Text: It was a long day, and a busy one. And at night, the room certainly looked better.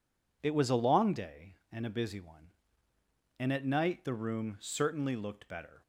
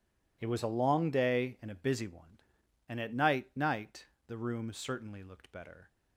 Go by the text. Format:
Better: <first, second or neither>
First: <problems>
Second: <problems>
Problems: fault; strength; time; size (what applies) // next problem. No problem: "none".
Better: first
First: none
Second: says "night" twice; at 3.5 s